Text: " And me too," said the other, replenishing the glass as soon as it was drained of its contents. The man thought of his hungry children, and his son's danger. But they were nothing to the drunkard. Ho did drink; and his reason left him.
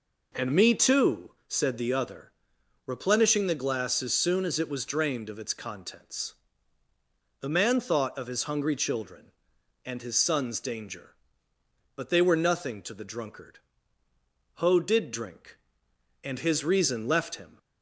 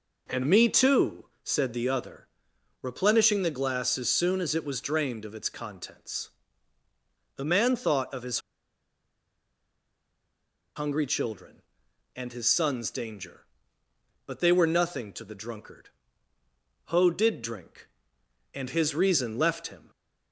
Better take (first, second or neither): first